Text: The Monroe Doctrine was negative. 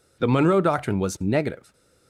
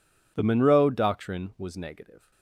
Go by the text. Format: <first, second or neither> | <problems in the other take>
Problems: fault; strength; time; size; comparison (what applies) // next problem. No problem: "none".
neither | none